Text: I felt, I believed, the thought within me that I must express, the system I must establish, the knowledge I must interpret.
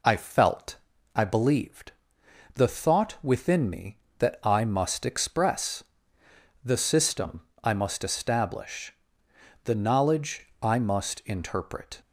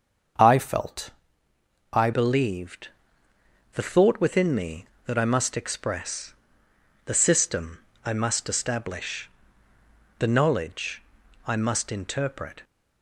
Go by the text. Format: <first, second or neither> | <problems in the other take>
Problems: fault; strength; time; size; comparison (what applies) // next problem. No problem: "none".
first | starts louder than the rest; until 2.2 s; 7 dB // changes voice at "believed"; from 2.1 s on; 10.5 s long // pauses between "system" and "I"; slight; at 7.7 s; 0.26 s long; slight in the first // pauses between "knowledge" and "I"; noticeable; at 11.0 s; 0.46 s long; slight in the first